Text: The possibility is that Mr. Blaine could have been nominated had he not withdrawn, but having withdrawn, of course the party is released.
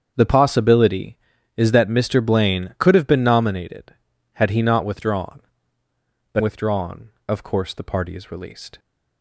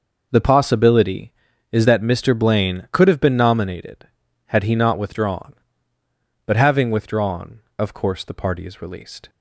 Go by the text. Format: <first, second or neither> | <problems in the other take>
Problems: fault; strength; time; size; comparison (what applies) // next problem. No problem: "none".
second | starts louder than the rest; strong; until 1.1 s; 7.5 dB // skips "having"; at 6.4 s